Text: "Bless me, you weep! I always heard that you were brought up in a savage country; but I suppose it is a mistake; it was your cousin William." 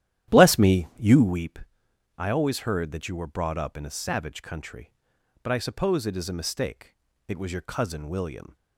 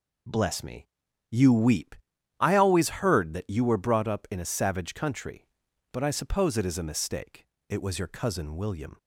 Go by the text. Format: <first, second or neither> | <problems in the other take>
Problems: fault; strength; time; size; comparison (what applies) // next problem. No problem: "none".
second | starts louder than the rest; strong; until 1.4 s; 12 dB